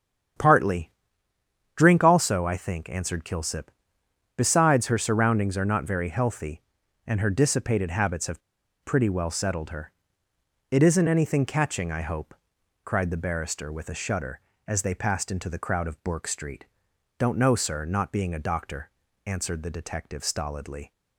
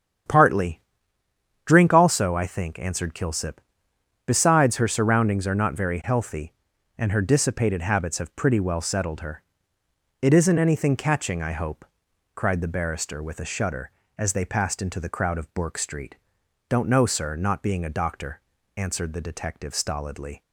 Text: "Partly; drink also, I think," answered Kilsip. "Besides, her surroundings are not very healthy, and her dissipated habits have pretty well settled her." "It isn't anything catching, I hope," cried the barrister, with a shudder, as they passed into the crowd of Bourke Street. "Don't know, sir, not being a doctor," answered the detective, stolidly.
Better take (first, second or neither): second